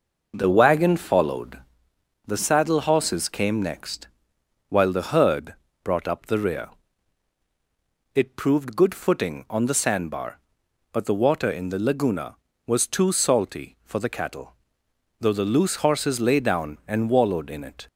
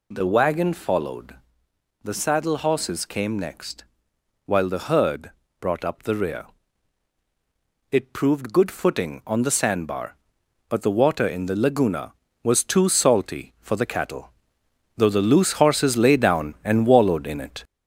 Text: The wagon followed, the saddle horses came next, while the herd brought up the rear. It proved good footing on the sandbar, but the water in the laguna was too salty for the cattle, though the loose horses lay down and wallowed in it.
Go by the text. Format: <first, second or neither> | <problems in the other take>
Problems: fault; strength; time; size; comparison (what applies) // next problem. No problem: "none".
first | gets louder; slight; throughout; 3 dB // pauses between "herd" and "brought"; slight; at 5.3 s; 0.30 s long; slight in the first